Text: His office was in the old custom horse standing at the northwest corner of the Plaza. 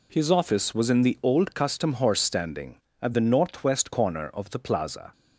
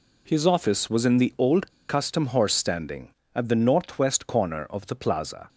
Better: first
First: none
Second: pauses between "old" and "custom"; slight; at 1.7 s; 0.18 s long

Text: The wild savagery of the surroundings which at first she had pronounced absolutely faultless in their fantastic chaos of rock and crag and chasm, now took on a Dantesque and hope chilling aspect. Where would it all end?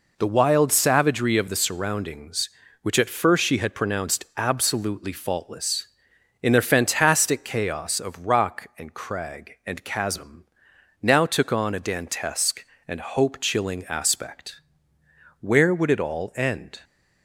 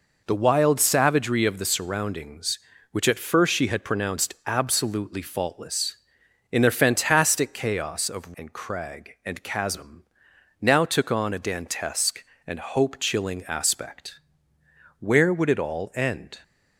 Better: first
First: none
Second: skips "rock"; at 8.3 s

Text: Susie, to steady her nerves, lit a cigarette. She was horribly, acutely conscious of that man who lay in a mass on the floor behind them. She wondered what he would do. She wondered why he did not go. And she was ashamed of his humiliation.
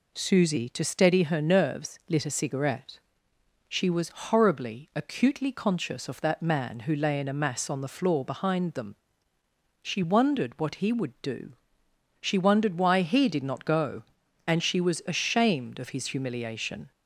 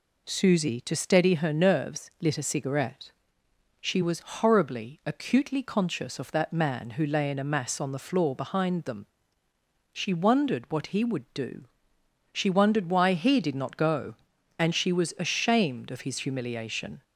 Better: neither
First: none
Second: none

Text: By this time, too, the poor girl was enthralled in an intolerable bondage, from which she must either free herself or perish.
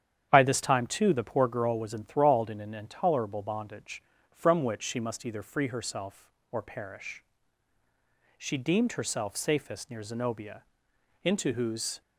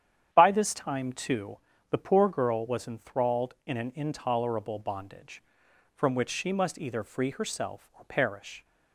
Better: second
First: starts louder than the rest; strong; until 1.3 s; 9 dB // goes on to say "She deemed herself safest near Zenobia into whose"; strong; from 8.3 s on; 3.6 s long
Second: starts louder than the rest; strong; until 1.3 s; 9 dB

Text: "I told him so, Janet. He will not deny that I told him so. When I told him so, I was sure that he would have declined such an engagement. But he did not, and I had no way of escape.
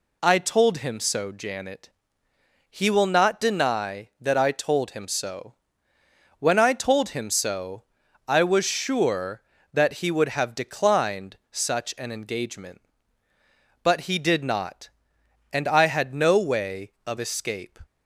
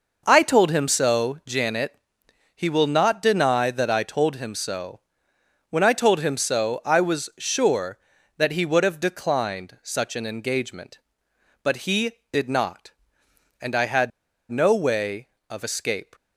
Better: first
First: none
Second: pauses between "had" and "no"; at 14.1 s; 0.40 s long

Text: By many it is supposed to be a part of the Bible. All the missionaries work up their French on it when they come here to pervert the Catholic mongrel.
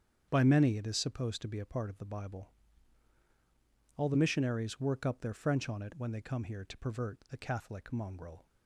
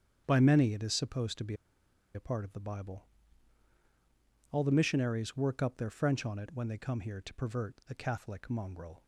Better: first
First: starts louder than the rest; strong; until 1.3 s; 8 dB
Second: starts louder than the rest; strong; until 1.2 s; 8 dB // pauses between "be" and "a"; noticeable; at 1.5 s; 0.60 s long

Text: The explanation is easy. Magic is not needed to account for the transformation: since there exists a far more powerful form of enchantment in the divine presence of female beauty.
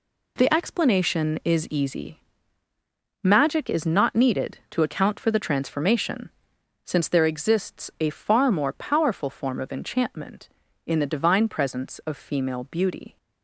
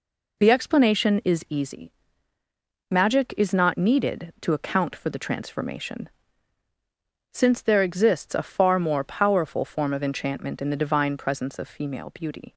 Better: neither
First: none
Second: none

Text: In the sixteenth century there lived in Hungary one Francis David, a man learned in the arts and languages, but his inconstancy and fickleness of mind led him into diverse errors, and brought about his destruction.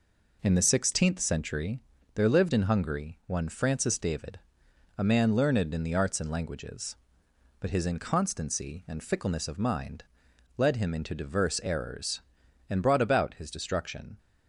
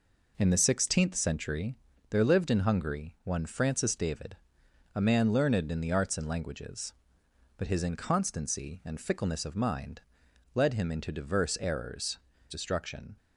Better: first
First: pauses between "century" and "there"; slight; at 1.8 s; 0.32 s long // pauses between "mind" and "led"; noticeable; at 10.0 s; 0.52 s long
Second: pauses between "century" and "there"; slight; at 1.7 s; 0.32 s long // pauses between "mind" and "led"; noticeable; at 10.0 s; 0.52 s long // skips "and brought about his"; at 12.3 s

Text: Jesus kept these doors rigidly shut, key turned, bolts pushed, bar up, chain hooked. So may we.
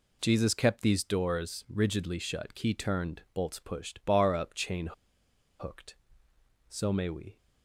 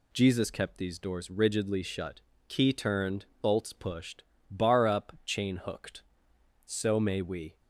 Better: second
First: pauses between "chain" and "hooked"; noticeable; at 4.9 s; 0.69 s long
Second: none

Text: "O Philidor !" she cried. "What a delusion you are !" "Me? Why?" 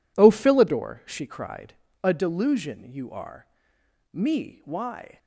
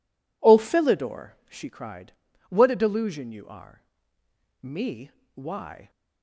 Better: second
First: skips "What"; at 1.8 s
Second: none

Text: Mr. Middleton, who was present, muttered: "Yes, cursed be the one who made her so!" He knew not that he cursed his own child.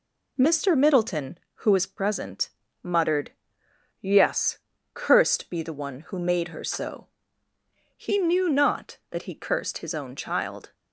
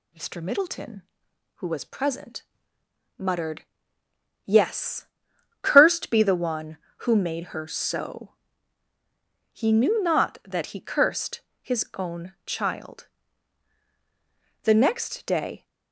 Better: first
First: none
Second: pauses between "cursed" and "his"; slight; at 11.4 s; 0.22 s long // goes on to say "The next day"; noticeable; from 14.6 s on; 1.0 s long

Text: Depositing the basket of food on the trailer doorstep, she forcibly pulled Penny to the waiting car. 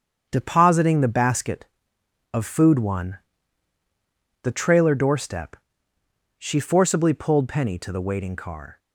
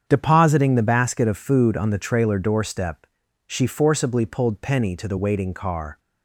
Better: second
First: starts louder than the rest; strong; until 1.3 s; 7.5 dB // says "one" for "on"; at 2.7 s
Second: starts louder than the rest; strong; until 1.0 s; 7.5 dB

